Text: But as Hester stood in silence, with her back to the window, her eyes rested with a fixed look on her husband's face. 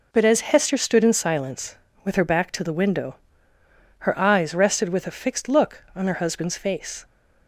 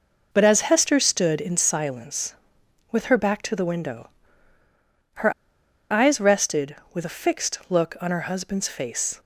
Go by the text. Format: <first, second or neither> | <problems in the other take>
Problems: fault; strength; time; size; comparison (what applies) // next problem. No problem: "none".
first | pauses between "her" and "eyes"; noticeable; at 5.3 s; 0.58 s long